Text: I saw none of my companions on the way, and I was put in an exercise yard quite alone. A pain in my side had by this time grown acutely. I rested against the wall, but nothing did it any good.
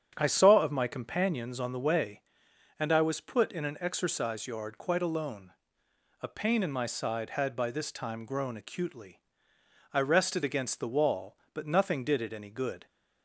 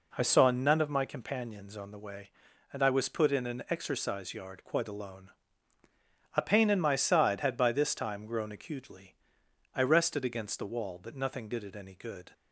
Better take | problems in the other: second | starts louder than the rest; strong; until 1.1 s; 8.5 dB // skips "none"; at 0.6 s

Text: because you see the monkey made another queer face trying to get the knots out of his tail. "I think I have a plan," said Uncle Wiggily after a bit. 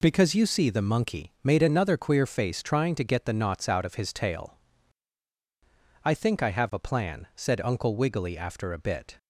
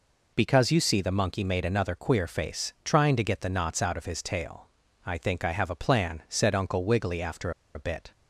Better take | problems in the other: first | pauses between "after" and "a"; slight; at 7.5 s; 0.23 s long

